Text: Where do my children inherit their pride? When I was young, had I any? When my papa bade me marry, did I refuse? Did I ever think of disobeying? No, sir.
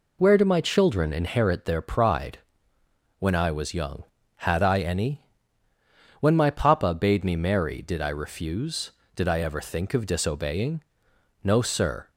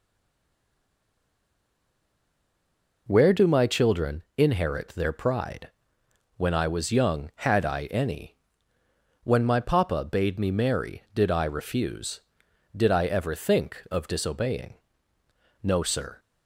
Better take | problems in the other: first | stays silent before the first word; strong; until 3.0 s; 3.0 s long

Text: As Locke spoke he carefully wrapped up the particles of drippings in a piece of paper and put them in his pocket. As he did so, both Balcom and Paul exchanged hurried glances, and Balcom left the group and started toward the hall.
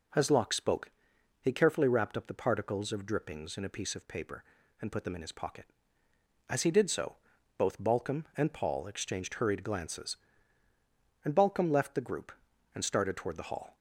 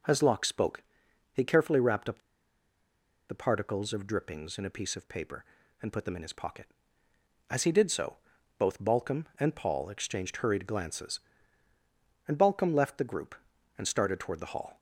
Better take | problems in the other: first | pauses between "spoke" and "he"; noticeable; at 0.8 s; 0.50 s long; noticeable in the first // pauses between "up" and "the"; at 2.1 s; 1.1 s long

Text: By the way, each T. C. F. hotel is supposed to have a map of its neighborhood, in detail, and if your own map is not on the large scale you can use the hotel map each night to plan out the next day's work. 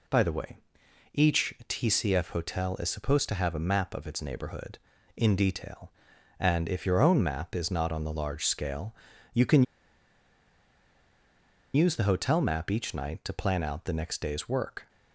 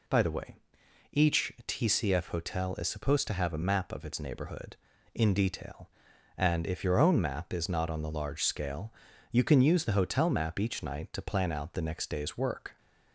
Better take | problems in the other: second | pauses between "scale" and "you"; at 8.9 s; 0.38 s long; also in the second // pauses between "can" and "use"; strong; at 9.6 s; 2.1 s long

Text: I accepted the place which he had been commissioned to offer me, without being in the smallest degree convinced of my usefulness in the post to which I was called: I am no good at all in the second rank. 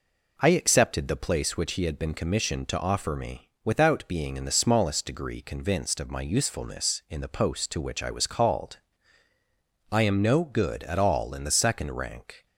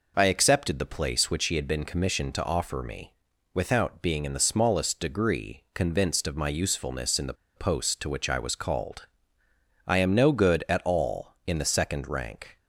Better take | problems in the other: first | pauses between "the" and "post"; slight; at 7.3 s; 0.22 s long

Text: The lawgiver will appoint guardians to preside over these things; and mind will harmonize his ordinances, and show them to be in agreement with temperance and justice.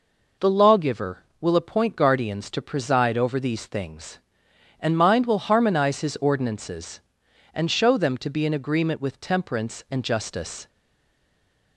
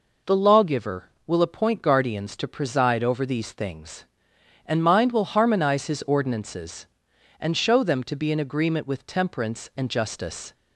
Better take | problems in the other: second | stays silent after the last word; from 10.6 s on; 1.1 s long

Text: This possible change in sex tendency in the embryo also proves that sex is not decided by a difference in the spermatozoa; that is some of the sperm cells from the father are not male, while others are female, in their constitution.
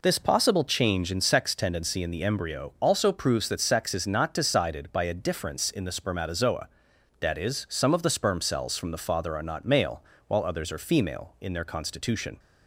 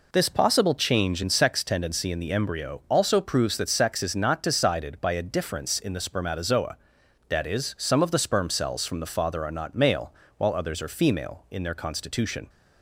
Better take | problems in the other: neither | none

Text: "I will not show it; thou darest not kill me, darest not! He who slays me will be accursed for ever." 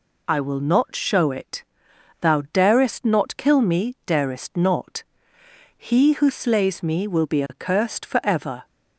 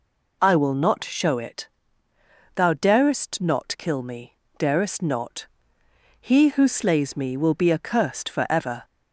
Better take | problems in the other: neither | none

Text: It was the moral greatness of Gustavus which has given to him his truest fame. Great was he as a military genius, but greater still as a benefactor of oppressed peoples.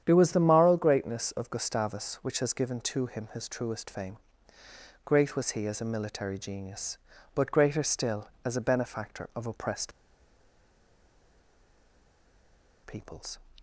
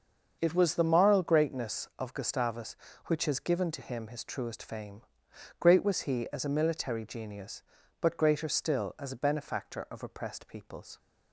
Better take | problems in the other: second | starts louder than the rest; strong; until 1.0 s; 9 dB; also in the second // pauses between "oppressed" and "peoples"; strong; at 9.9 s; 2.9 s long

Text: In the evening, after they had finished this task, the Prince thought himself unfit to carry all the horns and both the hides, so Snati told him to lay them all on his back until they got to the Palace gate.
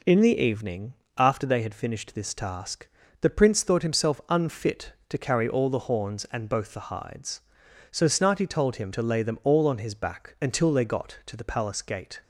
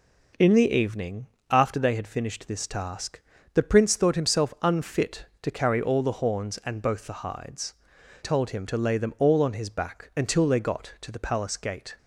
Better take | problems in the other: first | skips "so Snati"; at 7.9 s

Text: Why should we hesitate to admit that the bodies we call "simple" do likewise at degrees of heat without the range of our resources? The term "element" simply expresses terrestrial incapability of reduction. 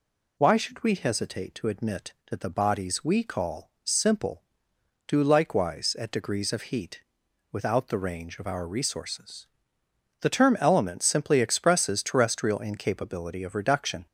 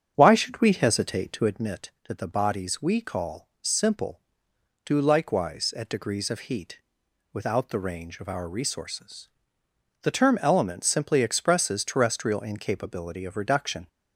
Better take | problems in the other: first | starts louder than the rest; strong; until 1.6 s; 8 dB // pauses between "heat" and "without"; noticeable; at 6.7 s; 0.55 s long; noticeable in the first

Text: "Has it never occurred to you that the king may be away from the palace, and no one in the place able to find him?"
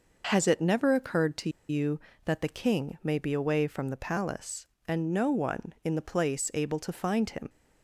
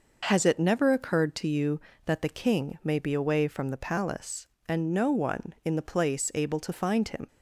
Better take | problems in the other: second | pauses between "to" and "you"; slight; at 1.4 s; 0.19 s long

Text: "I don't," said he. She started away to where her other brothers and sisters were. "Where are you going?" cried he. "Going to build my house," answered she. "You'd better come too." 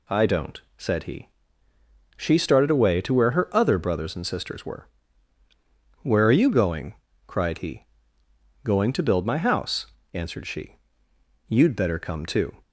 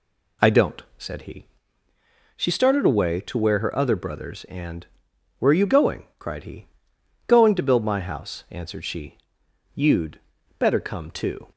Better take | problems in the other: first | skips "sisters were"; at 5.1 s // pauses between "You'd" and "better"; at 10.1 s; 0.38 s long

